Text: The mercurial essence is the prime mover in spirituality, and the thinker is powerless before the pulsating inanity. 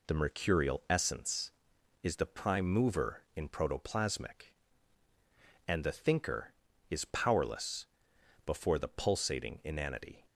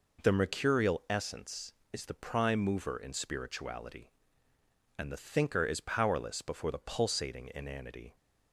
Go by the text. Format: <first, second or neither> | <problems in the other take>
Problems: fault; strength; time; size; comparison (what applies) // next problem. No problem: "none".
second | says "protoplasmic" for "spirituality"; at 3.4 s // pauses between "powerless" and "before"; noticeable; at 7.8 s; 0.58 s long